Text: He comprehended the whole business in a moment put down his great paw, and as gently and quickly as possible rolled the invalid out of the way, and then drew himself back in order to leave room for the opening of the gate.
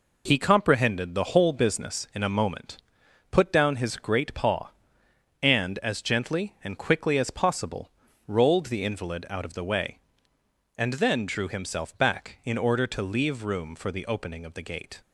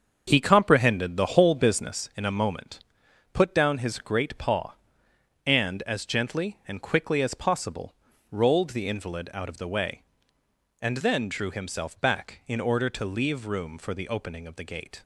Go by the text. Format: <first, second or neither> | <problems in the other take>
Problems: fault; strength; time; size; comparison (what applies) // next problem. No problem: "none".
first | starts louder than the rest; until 2.0 s; 7 dB // pauses between "moment" and "put"; noticeable; at 2.8 s; 0.52 s long; noticeable in the first // pauses between "possible" and "rolled"; slight; at 7.9 s; 0.36 s long; slight in the first